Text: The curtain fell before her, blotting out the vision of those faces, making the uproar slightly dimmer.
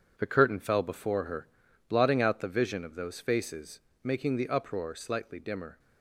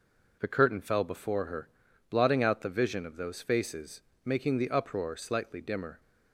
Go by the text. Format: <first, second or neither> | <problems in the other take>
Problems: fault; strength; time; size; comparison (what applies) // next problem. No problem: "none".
second | gets quieter; strong; throughout; 8.5 dB